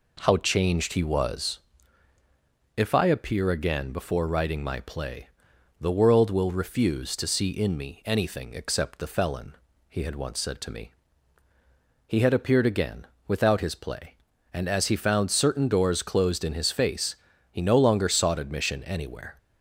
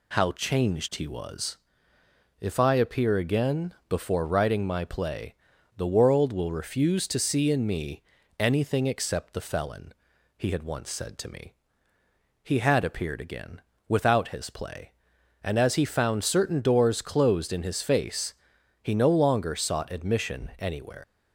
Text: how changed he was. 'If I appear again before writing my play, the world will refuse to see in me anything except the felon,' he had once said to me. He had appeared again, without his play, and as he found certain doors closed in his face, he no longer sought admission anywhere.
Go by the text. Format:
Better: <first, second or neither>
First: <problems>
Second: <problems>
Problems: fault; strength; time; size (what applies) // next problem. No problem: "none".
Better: first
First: none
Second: pauses between "me" and "anything"; at 8.0 s; 0.38 s long // leaves "anywhere" unfinished; at 21.0 s; 105 ms